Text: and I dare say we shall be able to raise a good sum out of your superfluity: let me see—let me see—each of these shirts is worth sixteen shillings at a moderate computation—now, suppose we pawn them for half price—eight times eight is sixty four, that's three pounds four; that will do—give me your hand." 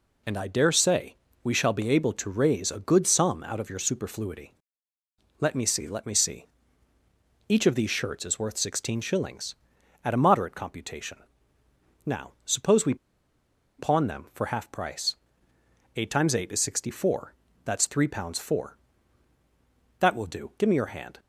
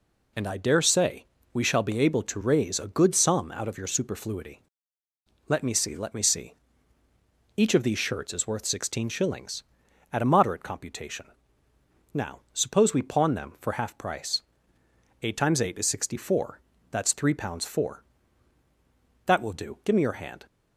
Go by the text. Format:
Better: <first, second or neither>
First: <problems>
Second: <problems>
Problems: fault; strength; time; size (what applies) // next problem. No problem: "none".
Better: second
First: pauses between "say" and "we"; slight; at 1.1 s; 0.28 s long // pauses between "we" and "pawn"; noticeable; at 12.9 s; 0.83 s long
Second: pauses between "say" and "we"; slight; at 1.2 s; 0.28 s long